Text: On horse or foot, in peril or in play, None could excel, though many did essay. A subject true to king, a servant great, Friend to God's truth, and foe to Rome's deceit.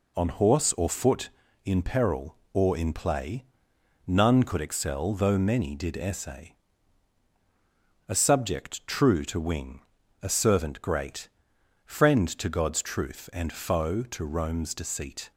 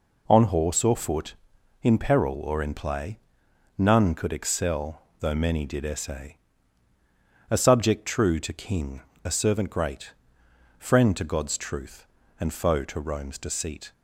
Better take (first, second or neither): second